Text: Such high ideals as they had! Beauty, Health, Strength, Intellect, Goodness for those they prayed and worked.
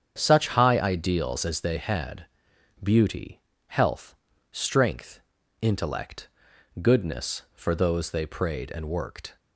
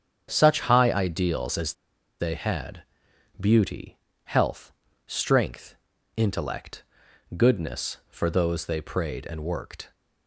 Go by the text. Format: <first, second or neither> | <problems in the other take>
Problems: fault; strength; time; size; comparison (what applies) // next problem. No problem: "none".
first | starts louder than the rest; strong; until 1.3 s; 8 dB; strong in the first // pauses between "as" and "they"; noticeable; at 1.7 s; 0.46 s long